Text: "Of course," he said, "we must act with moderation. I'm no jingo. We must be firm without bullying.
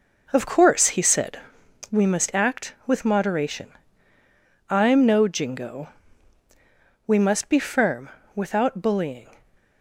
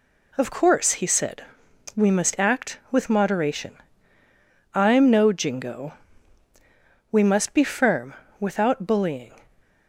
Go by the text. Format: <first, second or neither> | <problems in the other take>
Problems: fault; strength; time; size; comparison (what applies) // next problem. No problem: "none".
second | starts louder than the rest; noticeable; until 1.8 s; 5 dB // pauses between "firm" and "without"; slight; at 8.0 s; 0.24 s long; slight in the second